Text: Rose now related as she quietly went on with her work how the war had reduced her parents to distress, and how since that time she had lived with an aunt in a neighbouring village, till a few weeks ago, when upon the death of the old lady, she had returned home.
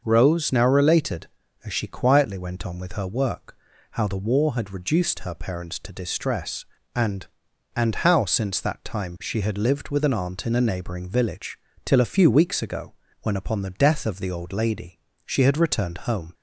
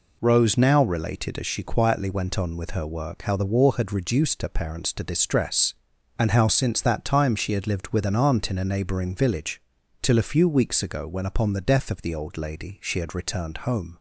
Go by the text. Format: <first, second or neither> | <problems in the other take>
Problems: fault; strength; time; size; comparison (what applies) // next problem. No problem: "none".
second | starts louder than the rest; until 1.0 s; 6 dB // pauses between "work" and "how"; slight; at 3.5 s; 0.36 s long // says "and" twice; at 7.7 s